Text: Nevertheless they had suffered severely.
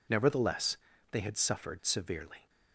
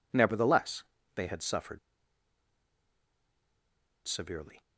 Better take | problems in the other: first | pauses between "Nevertheless" and "they"; slight; at 0.8 s; 0.30 s long; slight in the first // pauses between "suffered" and "severely"; strong; at 1.7 s; 2.2 s long

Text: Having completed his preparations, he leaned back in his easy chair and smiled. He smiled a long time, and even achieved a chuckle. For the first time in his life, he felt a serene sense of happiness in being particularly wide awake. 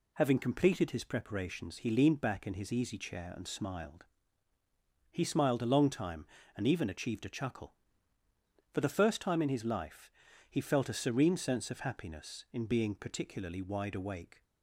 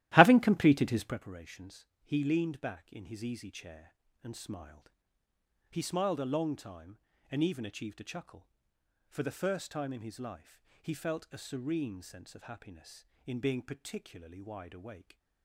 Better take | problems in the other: first | starts louder than the rest; strong; until 1.2 s; 14.5 dB

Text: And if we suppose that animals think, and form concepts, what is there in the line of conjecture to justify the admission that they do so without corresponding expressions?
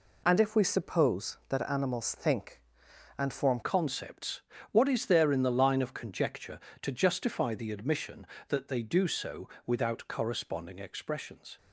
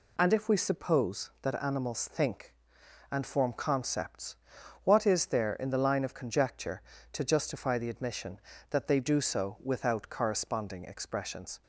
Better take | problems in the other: second | changes voice at "concepts"; from 3.6 s on; 7.9 s long // pauses between "so" and "without"; slight; at 9.4 s; 0.16 s long

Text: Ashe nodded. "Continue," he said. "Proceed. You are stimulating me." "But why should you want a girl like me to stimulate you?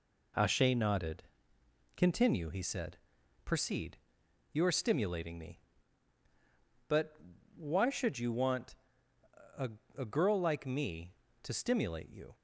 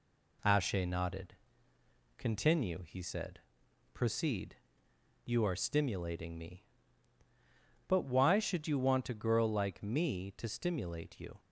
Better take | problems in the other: second | pauses between "But" and "why"; at 7.1 s; 0.38 s long // pauses between "want" and "a"; noticeable; at 8.7 s; 0.82 s long // says "a" twice; at 9.9 s

